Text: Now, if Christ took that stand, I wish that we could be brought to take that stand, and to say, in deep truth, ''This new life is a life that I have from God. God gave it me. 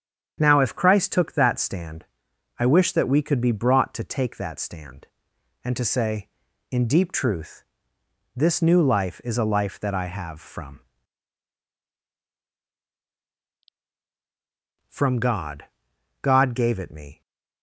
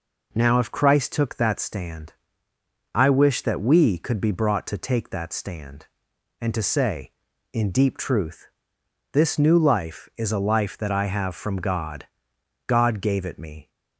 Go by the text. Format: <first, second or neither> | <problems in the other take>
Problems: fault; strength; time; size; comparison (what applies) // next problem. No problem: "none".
second | starts louder than the rest; strong; until 1.3 s; 8 dB // says "from" twice; at 14.8 s